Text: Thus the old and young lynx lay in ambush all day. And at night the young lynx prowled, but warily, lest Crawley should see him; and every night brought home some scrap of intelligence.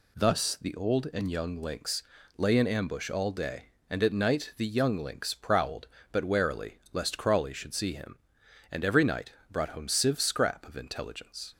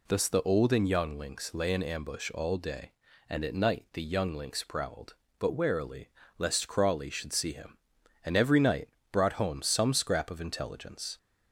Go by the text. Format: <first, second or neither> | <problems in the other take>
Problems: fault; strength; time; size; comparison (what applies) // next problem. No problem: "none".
second | pauses between "lynx" and "lay"; slight; at 2.0 s; 0.36 s long // pauses between "night" and "brought"; slight; at 9.3 s; 0.20 s long; slight in the second // says "sieve" for "some"; at 9.8 s